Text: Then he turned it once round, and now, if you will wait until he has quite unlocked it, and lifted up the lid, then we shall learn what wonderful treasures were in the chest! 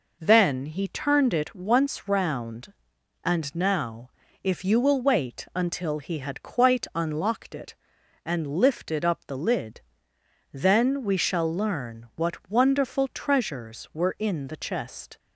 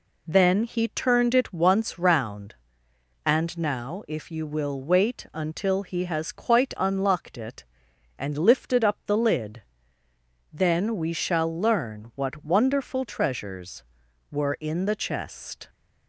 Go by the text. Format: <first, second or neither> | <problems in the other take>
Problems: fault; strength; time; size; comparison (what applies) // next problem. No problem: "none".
second | says "had" for "has"; at 6.1 s